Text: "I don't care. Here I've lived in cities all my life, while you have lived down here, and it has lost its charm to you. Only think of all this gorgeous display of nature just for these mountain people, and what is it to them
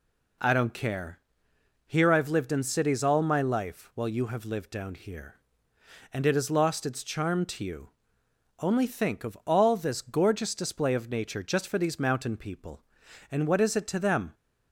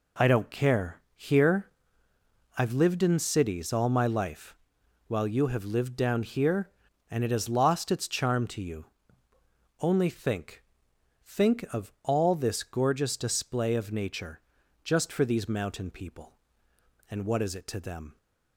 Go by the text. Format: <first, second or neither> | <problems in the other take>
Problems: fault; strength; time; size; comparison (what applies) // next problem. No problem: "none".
first | pauses between "Here" and "I've"; noticeable; at 1.6 s; 0.88 s long // says "think" twice; at 11.2 s // pauses between "nature" and "just"; at 14.4 s; 0.42 s long